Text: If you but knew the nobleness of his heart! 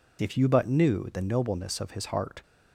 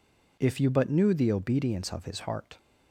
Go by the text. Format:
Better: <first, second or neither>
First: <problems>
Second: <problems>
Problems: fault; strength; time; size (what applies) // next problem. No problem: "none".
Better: first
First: none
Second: says "obedience" for "nobleness"; at 1.3 s